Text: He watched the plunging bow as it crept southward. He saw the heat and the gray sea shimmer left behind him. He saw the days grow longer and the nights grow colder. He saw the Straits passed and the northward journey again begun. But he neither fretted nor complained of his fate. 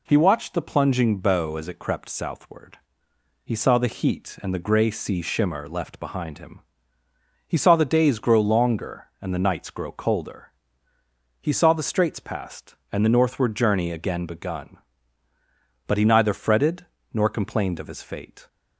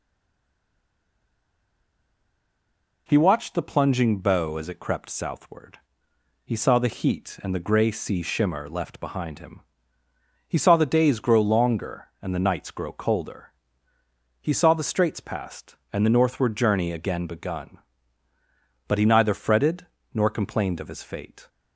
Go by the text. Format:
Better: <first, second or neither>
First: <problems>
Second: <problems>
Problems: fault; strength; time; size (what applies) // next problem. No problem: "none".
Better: first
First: pauses between "fretted" and "nor"; slight; at 16.8 s; 0.26 s long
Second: stays silent before the first word; strong; until 3.0 s; 3.0 s long // pauses between "fretted" and "nor"; slight; at 19.8 s; 0.26 s long